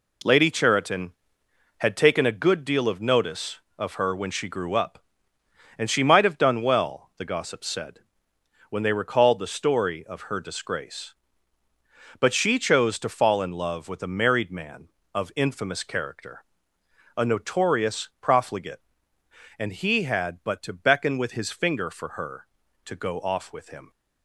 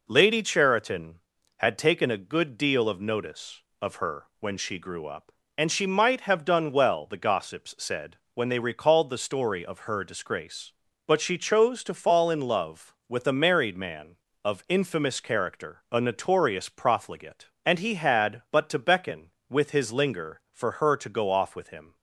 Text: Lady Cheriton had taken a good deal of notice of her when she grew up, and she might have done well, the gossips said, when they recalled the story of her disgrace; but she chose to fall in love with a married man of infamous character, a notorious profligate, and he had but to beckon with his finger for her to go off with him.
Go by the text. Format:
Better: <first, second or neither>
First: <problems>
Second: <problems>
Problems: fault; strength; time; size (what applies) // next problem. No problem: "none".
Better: first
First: none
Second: says "linger" for "finger"; at 19.9 s